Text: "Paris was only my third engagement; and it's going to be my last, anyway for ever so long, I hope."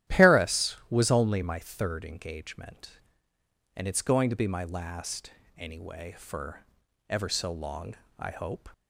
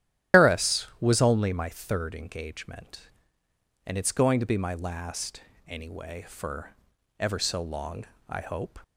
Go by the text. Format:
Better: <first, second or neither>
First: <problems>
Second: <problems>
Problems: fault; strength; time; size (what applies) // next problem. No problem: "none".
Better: first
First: starts louder than the rest; strong; until 1.2 s; 12 dB // pauses between "for" and "ever"; noticeable; at 6.6 s; 0.46 s long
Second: loses the start of "Paris"; at 0.3 s; 155 ms // starts louder than the rest; strong; until 1.4 s; 12 dB // pauses between "for" and "ever"; noticeable; at 6.7 s; 0.46 s long